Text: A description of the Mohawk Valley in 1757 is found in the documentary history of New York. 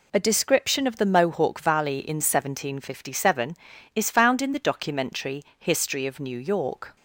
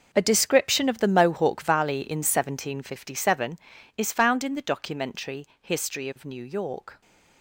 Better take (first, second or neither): first